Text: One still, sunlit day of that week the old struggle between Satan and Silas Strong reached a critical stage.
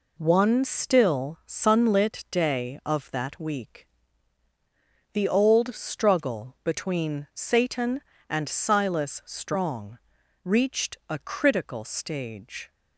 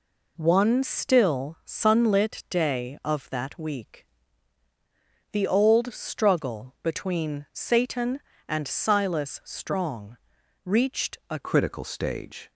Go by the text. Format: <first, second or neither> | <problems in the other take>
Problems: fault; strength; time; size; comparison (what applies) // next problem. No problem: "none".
first | pauses between "week" and "the"; strong; at 4.0 s; 1.2 s long; strong in the first // pauses between "Strong" and "reached"; at 10.1 s; 0.44 s long; also in the first // changes voice at "critical"; from 11.3 s on; 1.2 s long